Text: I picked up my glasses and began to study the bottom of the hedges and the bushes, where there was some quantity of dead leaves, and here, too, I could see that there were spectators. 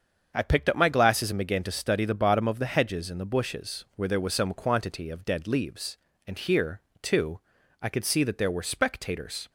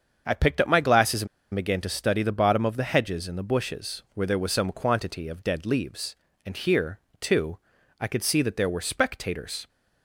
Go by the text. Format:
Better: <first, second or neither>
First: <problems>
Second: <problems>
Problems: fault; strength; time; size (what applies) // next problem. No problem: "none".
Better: first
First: starts louder than the rest; strong; until 1.3 s; 7 dB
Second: starts louder than the rest; strong; until 1.2 s; 7 dB // pauses between "and" and "began"; slight; at 1.2 s; 0.26 s long